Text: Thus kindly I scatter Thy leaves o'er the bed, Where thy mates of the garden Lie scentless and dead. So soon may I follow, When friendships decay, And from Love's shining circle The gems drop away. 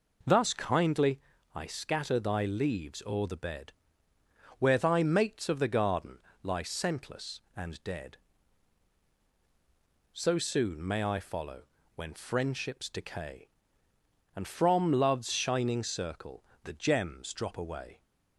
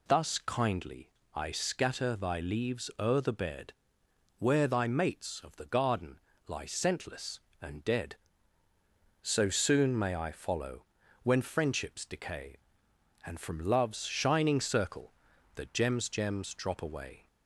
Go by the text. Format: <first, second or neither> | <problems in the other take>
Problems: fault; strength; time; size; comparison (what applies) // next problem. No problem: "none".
first | pauses between "kindly" and "I"; slight; at 1.0 s; 0.26 s long; slight in the first // pauses between "garden" and "Lie"; slight; at 6.1 s; 0.28 s long; slight in the first // pauses between "circle" and "The"; at 15.1 s; 0.42 s long; slight in the first // says "gems" twice; at 16.0 s